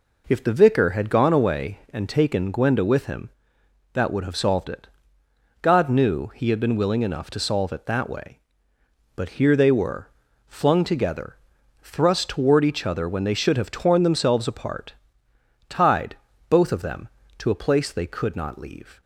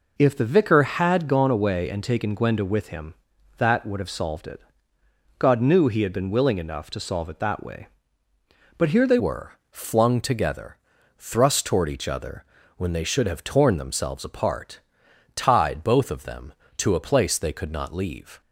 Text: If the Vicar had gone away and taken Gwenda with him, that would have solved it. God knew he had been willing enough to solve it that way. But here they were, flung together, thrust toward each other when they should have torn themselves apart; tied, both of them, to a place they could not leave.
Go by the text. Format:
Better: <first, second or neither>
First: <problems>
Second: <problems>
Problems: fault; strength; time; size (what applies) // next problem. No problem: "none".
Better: first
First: none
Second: changes voice at "were"; from 9.1 s on; 9.3 s long // pauses between "other" and "when"; slight; at 12.4 s; 0.32 s long